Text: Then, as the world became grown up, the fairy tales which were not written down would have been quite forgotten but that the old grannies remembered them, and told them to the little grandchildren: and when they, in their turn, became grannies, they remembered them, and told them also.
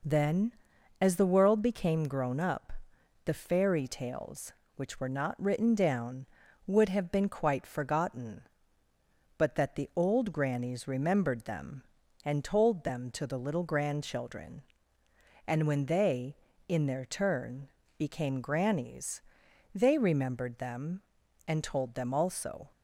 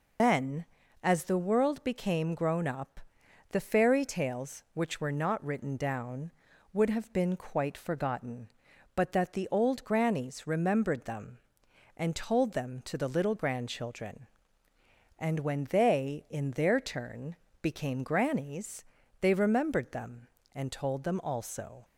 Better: first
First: none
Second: loses the start of "Then"; at 0.1 s; 155 ms

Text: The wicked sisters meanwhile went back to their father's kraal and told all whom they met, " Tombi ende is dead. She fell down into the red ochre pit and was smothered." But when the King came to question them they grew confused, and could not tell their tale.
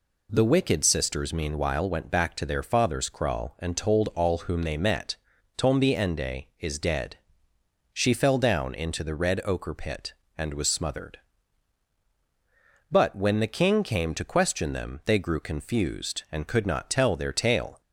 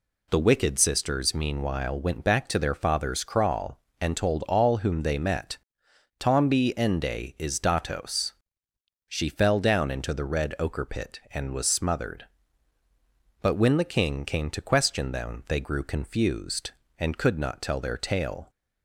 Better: first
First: none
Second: says "datos" for "dead"; at 7.5 s

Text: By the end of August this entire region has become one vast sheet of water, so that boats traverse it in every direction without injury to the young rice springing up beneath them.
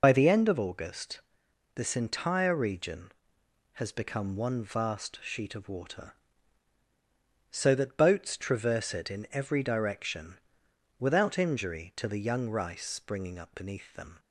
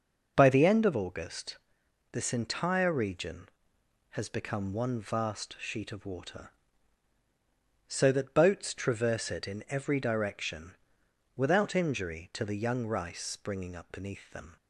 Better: second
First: loses the start of "By"; at 0.0 s; 45 ms // pauses between "August" and "this"; noticeable; at 1.2 s; 0.52 s long // pauses between "direction" and "without"; noticeable; at 10.3 s; 0.62 s long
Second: pauses between "August" and "this"; noticeable; at 1.5 s; 0.52 s long // pauses between "direction" and "without"; noticeable; at 10.7 s; 0.62 s long

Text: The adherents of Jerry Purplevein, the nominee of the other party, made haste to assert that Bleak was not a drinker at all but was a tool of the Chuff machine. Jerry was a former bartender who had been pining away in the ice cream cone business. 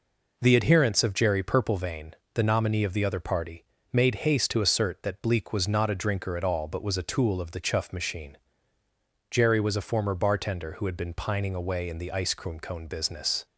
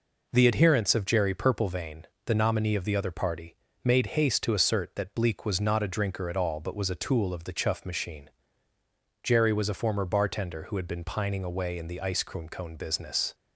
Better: neither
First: none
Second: none

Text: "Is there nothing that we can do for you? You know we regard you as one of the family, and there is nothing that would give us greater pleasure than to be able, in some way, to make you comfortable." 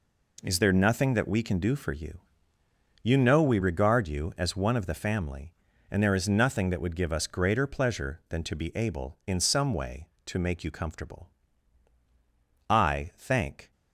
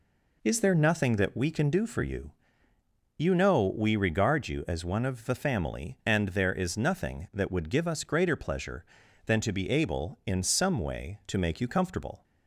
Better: second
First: goes on to say "I thank"; noticeable; from 12.6 s on; 1.0 s long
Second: none

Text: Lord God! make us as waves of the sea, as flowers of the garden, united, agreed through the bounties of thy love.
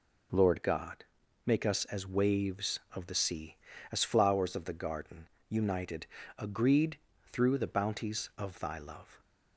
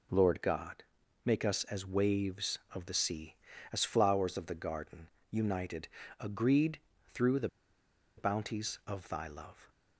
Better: first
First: pauses between "agreed" and "through"; slight; at 6.9 s; 0.34 s long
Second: pauses between "agreed" and "through"; slight; at 6.7 s; 0.34 s long // pauses between "the" and "bounties"; noticeable; at 7.4 s; 0.69 s long

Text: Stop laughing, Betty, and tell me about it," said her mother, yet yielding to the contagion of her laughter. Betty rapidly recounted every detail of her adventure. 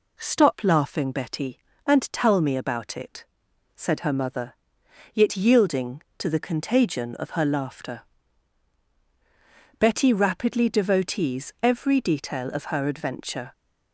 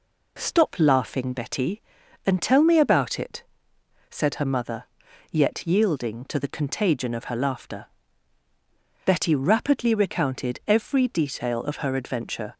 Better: second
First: says "devotees" for "recounted"; at 10.6 s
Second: none

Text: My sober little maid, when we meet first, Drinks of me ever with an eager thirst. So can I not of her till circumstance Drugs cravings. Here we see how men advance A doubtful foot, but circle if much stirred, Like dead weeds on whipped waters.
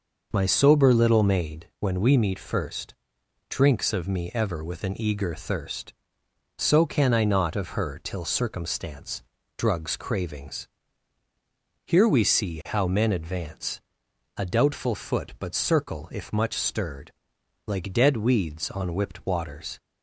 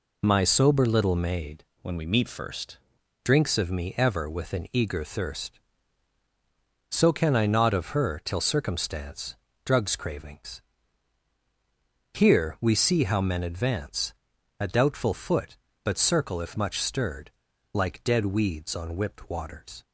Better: first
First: pauses between "circumstance" and "Drugs"; slight; at 9.2 s; 0.36 s long // pauses between "advance" and "A"; noticeable; at 13.7 s; 0.56 s long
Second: changes voice from "when" to "first"; from 1.8 to 2.7 s; 0.9 s long // pauses between "circumstance" and "Drugs"; slight; at 9.3 s; 0.28 s long // pauses between "advance" and "A"; noticeable; at 14.1 s; 0.48 s long

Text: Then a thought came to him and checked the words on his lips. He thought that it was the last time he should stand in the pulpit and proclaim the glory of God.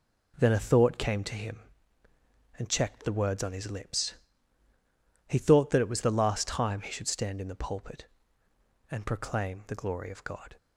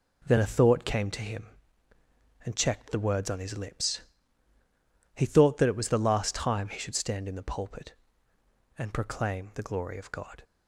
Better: neither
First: none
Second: none

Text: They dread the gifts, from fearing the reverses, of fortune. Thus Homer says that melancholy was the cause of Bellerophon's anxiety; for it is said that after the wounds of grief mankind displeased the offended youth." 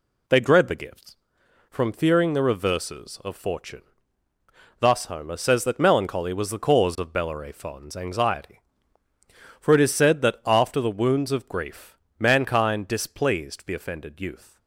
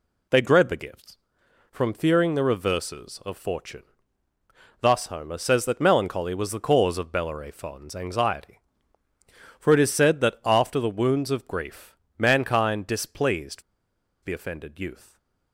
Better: first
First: pauses between "grief" and "mankind"; slight; at 11.9 s; 0.22 s long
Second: pauses between "grief" and "mankind"; slight; at 11.9 s; 0.22 s long // pauses between "displeased" and "the"; noticeable; at 13.6 s; 0.60 s long

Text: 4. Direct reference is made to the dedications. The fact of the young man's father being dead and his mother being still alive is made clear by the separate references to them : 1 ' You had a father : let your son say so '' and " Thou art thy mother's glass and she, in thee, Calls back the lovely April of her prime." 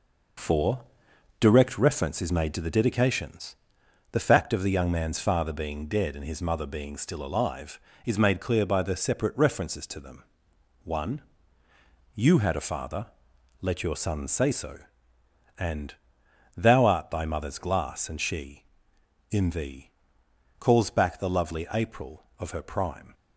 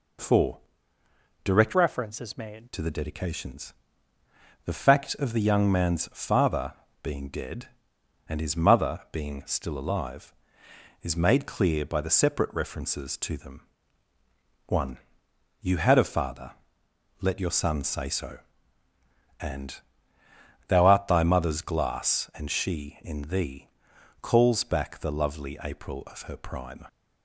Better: first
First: none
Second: changes voice from "reference" to "made"; from 1.7 to 2.6 s; 0.9 s long // pauses between "father" and "being"; slight; at 6.7 s; 0.26 s long

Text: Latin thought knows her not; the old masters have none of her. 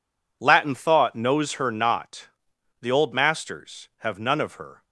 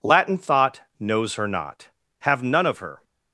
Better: first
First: none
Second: pauses between "thought" and "knows"; slight; at 0.8 s; 0.16 s long // skips "the old masters"; at 2.0 s

